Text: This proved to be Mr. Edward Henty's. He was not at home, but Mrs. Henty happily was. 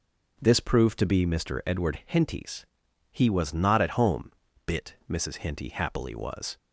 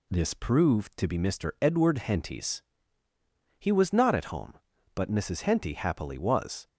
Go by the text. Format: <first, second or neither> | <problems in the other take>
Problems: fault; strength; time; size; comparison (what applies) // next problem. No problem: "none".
second | says "bit" for "but"; at 4.6 s